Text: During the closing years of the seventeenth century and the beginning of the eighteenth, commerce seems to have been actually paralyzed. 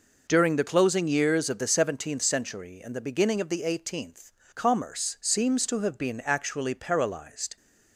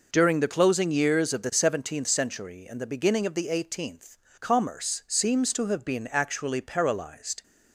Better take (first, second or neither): neither